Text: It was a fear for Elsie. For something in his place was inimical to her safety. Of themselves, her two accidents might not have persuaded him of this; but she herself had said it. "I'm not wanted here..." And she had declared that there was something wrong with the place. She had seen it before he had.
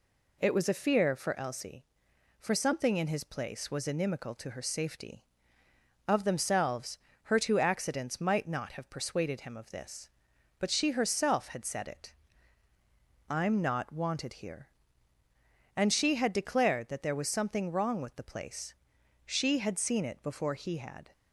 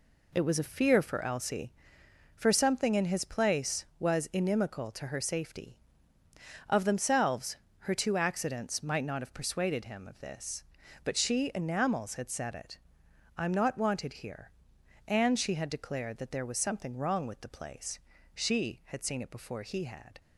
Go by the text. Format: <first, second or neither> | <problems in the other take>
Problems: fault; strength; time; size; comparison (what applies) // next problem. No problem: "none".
first | says "enamels" for "herself"; at 11.5 s